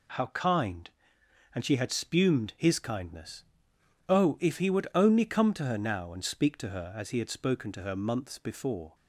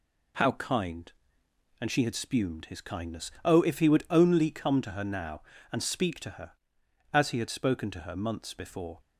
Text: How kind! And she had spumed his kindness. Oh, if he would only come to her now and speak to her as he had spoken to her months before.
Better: neither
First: none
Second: none

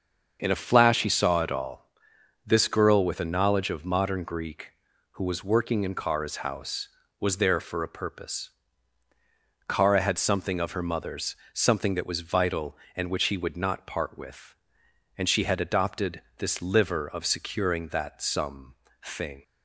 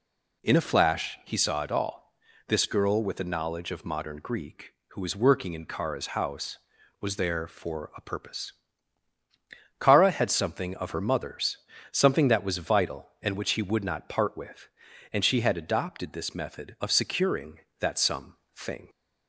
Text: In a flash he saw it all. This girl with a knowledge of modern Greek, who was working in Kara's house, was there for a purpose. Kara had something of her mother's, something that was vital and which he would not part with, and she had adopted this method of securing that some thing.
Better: second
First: starts louder than the rest; until 1.4 s; 6.5 dB // pauses between "adopted" and "this"; slight; at 16.2 s; 0.16 s long // says "liver" for "method"; at 16.6 s // pauses between "some" and "thing"; slight; at 18.7 s; 0.32 s long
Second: pauses between "some" and "thing"; slight; at 18.3 s; 0.20 s long

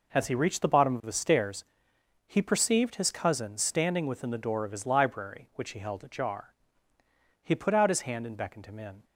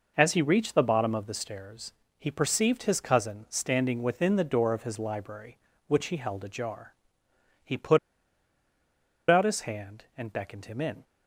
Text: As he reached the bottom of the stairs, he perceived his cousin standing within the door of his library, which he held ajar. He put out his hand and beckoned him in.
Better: first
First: none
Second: pauses between "put" and "out"; strong; at 7.9 s; 1.3 s long

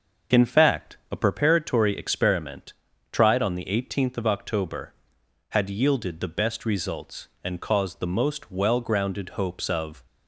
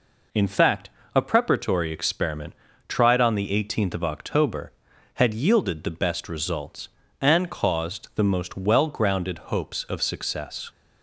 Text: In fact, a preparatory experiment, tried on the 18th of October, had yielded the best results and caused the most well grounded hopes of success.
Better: second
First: starts louder than the rest; until 1.4 s; 6.5 dB // stops before "success"; at 10.0 s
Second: none

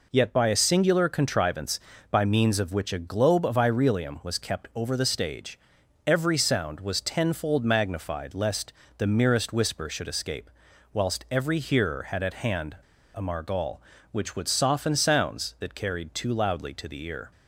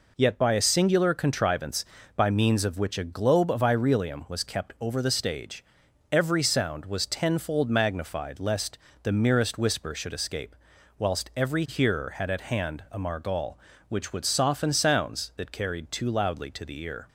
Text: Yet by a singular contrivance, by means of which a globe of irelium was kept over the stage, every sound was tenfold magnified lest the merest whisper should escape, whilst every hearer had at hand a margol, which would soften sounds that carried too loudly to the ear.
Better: second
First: pauses between "lest" and "the"; slight; at 8.7 s; 0.26 s long // pauses between "hand" and "a"; at 12.7 s; 0.38 s long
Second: pauses between "lest" and "the"; slight; at 8.7 s; 0.26 s long

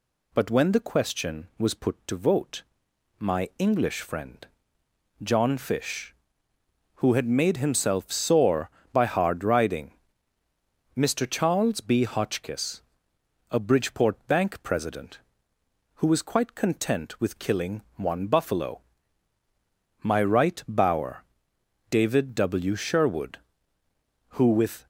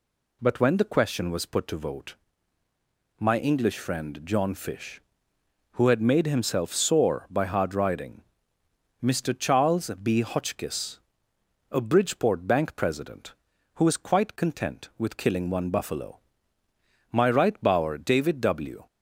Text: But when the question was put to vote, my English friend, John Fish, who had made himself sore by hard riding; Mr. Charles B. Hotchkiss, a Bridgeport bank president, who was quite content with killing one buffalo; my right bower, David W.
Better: second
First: goes on to say "Sherwood who with"; strong; from 22.7 s on; 2.1 s long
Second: none

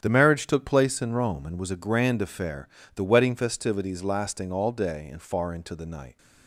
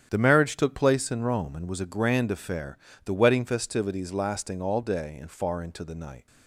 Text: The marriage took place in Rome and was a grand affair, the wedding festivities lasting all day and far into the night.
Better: neither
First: starts louder than the rest; strong; until 1.0 s; 9 dB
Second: starts louder than the rest; strong; until 1.1 s; 9 dB

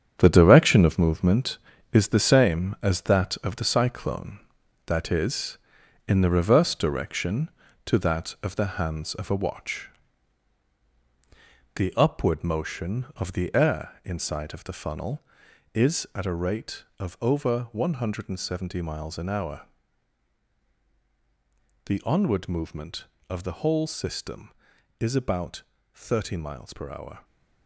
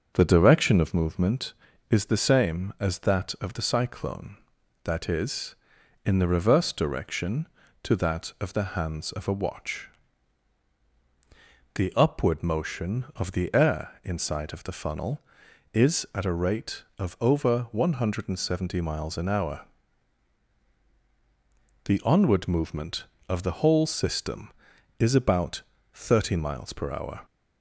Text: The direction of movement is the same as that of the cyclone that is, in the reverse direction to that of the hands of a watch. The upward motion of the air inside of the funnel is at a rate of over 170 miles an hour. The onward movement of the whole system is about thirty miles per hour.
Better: second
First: gets quieter; strong; throughout; 9.5 dB // starts louder than the rest; strong; until 1.2 s; 8.5 dB // pauses between "about" and "thirty"; slight; at 25.6 s; 0.32 s long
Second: starts louder than the rest; until 1.1 s; 6.5 dB // pauses between "about" and "thirty"; slight; at 25.6 s; 0.32 s long

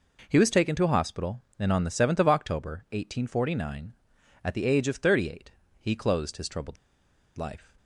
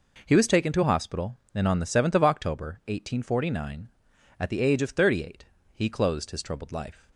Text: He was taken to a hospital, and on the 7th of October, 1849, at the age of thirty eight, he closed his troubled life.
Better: second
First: pauses between "troubled" and "life"; noticeable; at 6.7 s; 0.61 s long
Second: none

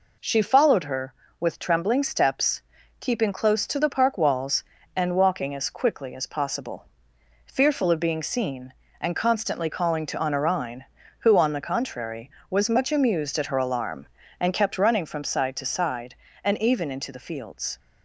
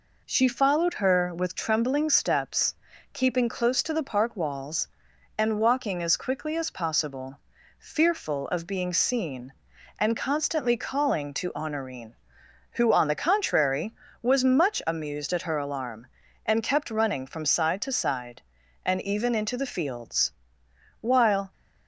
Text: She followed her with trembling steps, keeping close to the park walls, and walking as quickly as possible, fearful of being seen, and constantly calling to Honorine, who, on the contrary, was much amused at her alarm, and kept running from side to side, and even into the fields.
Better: first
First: none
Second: goes on to say "While"; from 21.0 s on; 0.50 s long

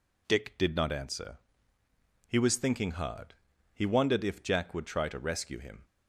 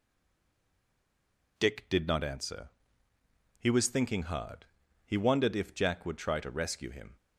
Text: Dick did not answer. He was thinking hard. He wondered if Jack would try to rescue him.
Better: first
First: none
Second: stays silent before the first word; noticeable; until 1.5 s; 1.5 s long

